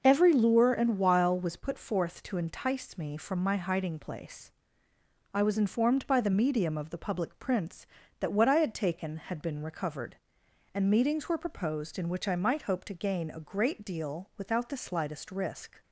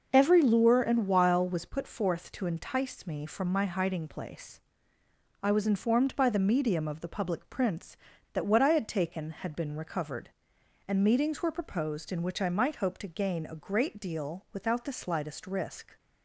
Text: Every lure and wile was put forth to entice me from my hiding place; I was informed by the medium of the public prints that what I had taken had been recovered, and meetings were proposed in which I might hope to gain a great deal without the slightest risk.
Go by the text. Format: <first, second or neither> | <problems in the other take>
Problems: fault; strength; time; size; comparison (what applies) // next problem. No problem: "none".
neither | none